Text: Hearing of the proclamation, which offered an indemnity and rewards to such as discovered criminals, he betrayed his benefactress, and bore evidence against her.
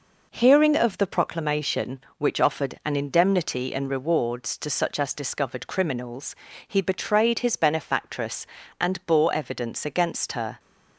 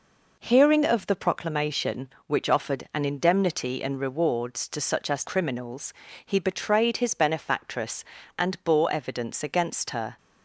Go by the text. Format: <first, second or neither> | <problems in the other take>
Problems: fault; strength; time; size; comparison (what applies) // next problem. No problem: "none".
first | skips "discovered"; at 5.2 s